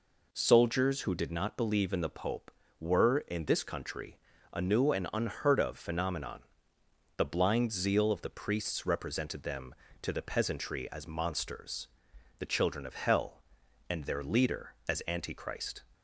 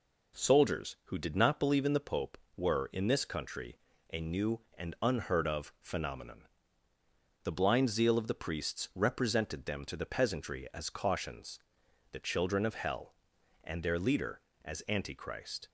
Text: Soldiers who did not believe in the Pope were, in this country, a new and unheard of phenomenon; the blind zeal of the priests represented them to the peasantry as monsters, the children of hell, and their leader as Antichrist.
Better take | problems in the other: first | says "cautions" for "monsters"; at 10.9 s

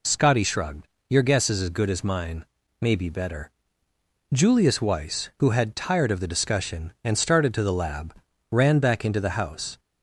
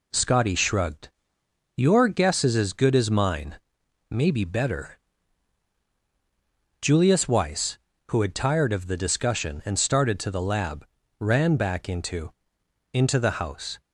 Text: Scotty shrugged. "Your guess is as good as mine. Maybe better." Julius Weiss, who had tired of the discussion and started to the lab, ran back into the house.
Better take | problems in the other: first | says "into" twice; at 12.9 s

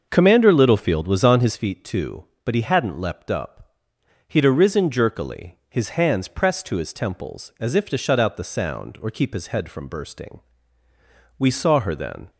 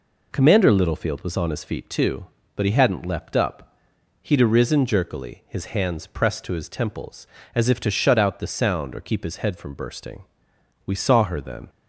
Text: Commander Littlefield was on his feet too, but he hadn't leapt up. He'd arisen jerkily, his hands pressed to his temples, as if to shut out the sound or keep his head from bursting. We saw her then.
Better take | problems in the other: second | starts louder than the rest; until 1.7 s; 6.5 dB

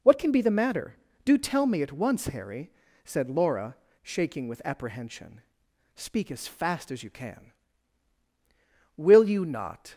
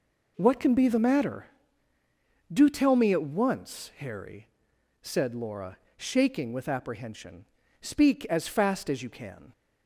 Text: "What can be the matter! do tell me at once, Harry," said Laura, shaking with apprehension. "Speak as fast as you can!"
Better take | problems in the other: second | goes on to say "Will you not"; noticeable; from 8.9 s on; 0.96 s long

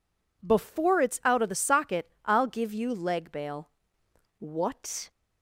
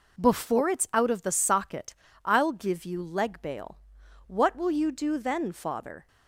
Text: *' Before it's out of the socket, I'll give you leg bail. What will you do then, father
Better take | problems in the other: second | stops before "will you do then father"; at 5.1 s

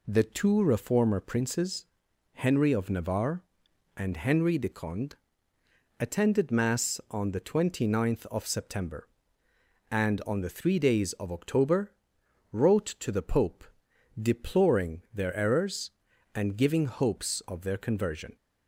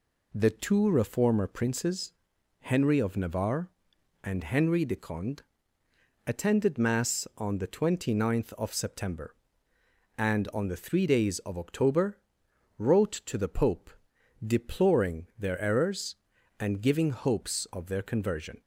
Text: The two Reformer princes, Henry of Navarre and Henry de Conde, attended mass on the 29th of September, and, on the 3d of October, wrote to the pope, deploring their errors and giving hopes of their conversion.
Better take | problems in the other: neither | none

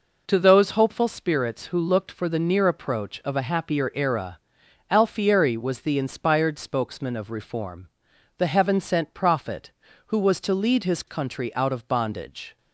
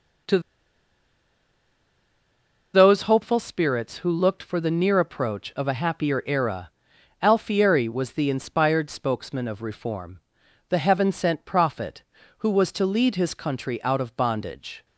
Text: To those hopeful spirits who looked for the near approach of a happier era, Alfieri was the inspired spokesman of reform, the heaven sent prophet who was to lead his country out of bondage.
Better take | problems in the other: first | pauses between "To" and "those"; strong; at 0.3 s; 2.3 s long

